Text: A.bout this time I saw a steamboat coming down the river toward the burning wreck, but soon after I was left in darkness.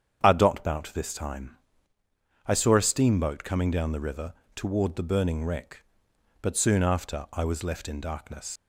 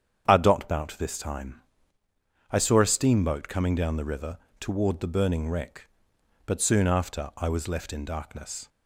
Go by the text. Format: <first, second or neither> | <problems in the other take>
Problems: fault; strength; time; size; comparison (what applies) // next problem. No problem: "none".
second | starts louder than the rest; strong; until 1.2 s; 8 dB; strong in the second // pauses between "time" and "I"; noticeable; at 1.5 s; 0.90 s long; noticeable in the second // pauses between "river" and "toward"; slight; at 4.3 s; 0.20 s long; slight in the second // leaves "darkness" unfinished; at 8.5 s; 80 ms